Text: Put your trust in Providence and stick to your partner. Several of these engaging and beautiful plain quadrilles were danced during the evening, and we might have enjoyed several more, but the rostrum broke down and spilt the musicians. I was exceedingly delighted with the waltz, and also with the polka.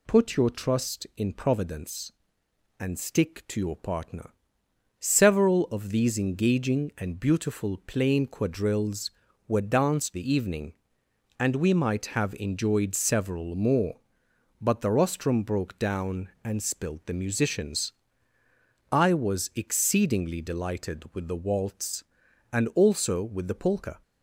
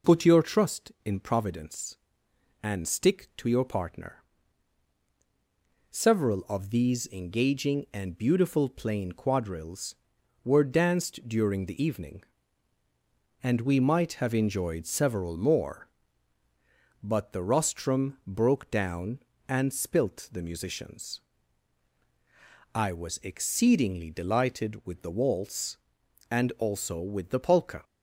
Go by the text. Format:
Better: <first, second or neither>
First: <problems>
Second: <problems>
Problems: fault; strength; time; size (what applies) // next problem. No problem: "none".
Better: second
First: skips "during"; at 10.1 s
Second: none